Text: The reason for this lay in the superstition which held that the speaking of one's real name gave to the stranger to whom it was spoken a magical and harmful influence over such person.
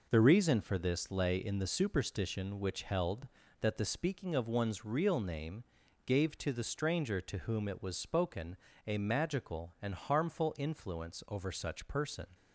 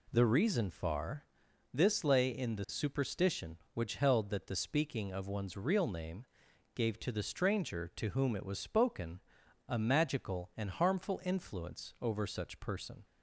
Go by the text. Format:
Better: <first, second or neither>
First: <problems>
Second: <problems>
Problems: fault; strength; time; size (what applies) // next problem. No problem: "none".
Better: first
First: pauses between "name" and "gave"; at 5.6 s; 0.42 s long // pauses between "spoken" and "a"; slight; at 8.5 s; 0.30 s long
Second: says "far" for "for"; at 0.7 s // pauses between "name" and "gave"; noticeable; at 6.2 s; 0.50 s long // pauses between "spoken" and "a"; noticeable; at 9.2 s; 0.46 s long